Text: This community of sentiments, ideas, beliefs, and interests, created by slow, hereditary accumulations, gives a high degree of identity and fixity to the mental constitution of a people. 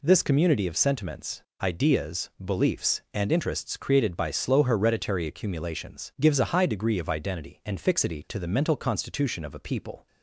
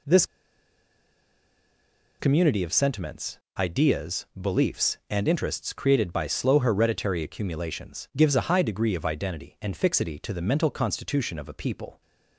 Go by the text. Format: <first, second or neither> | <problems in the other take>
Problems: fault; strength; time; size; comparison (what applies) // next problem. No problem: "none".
first | pauses between "This" and "community"; strong; at 0.2 s; 1.9 s long